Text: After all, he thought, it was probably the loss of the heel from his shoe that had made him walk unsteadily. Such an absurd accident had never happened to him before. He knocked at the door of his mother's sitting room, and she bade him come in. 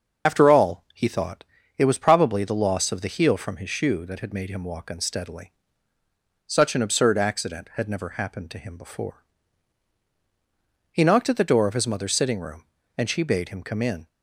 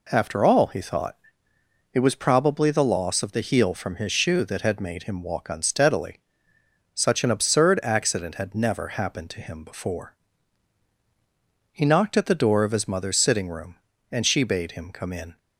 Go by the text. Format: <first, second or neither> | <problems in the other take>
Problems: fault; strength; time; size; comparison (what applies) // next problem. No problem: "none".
second | loses the start of "After"; at 0.2 s; 35 ms // starts louder than the rest; until 1.3 s; 6.5 dB